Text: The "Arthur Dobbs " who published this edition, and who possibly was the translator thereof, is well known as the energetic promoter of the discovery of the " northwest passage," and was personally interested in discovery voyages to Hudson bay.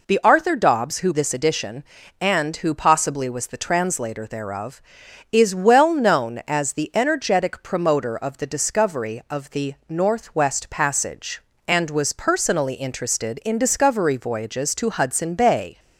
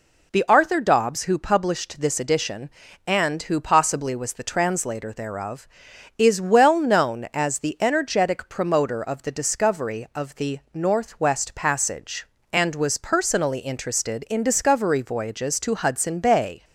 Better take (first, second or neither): second